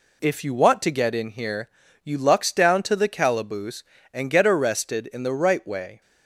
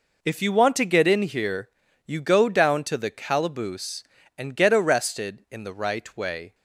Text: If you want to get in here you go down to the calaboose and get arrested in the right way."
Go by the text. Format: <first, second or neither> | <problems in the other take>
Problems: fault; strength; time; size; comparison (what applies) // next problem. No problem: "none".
second | pauses between "here" and "you"; slight; at 1.6 s; 0.34 s long; also in the second // says "lux" for "go"; at 2.1 s